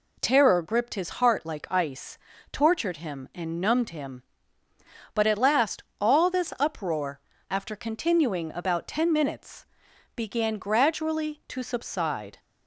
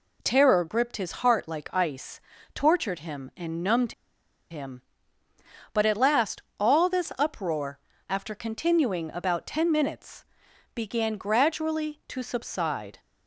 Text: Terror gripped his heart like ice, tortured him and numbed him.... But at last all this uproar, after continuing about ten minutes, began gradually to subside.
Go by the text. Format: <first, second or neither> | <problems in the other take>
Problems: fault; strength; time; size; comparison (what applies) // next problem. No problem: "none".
first | pauses between "numbed" and "him"; noticeable; at 3.9 s; 0.57 s long // pauses between "last" and "all"; slight; at 6.4 s; 0.18 s long; slight in the first